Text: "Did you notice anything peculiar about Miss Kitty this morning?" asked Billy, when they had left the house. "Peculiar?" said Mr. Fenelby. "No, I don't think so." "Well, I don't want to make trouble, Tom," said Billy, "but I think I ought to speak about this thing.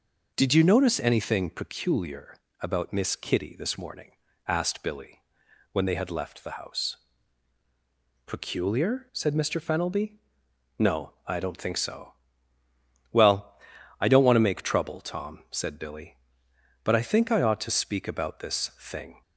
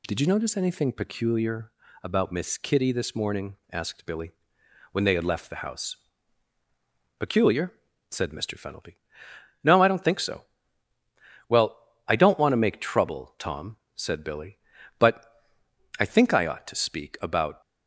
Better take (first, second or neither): first